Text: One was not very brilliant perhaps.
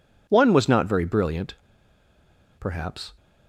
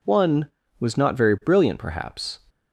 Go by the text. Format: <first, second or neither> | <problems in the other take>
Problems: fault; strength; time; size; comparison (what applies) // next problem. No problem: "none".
second | pauses between "brilliant" and "perhaps"; at 1.5 s; 1.0 s long